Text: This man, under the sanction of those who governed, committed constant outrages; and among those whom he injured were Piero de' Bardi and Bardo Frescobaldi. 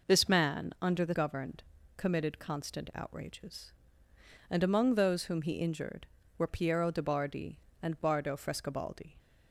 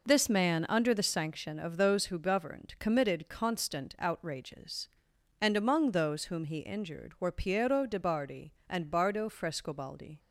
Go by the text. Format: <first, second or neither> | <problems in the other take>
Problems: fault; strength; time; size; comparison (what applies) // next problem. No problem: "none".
second | skips "sanction of those who"; at 1.1 s